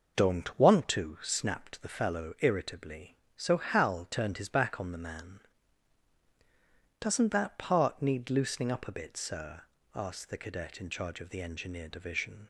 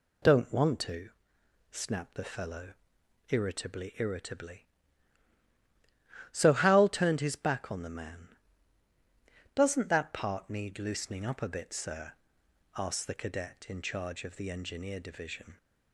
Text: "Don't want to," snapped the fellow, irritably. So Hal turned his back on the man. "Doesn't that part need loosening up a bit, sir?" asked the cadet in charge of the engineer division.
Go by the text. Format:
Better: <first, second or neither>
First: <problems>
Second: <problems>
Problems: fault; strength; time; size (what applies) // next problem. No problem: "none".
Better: first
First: none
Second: says "irritably" twice; at 3.9 s